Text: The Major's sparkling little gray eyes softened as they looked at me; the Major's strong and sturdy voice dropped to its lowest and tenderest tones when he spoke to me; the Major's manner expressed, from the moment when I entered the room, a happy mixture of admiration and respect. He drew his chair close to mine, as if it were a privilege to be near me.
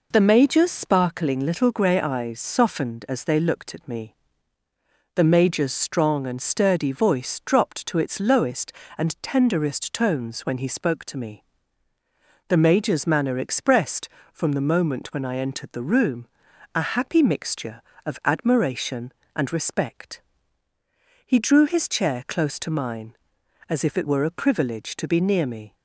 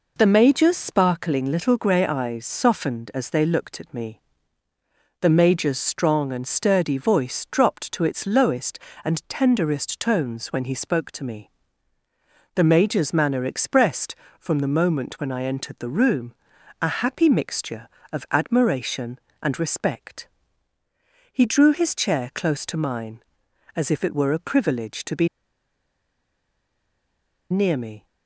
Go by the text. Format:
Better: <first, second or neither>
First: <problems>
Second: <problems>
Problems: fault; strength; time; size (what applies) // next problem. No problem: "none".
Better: first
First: none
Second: pauses between "be" and "near"; strong; at 25.2 s; 2.2 s long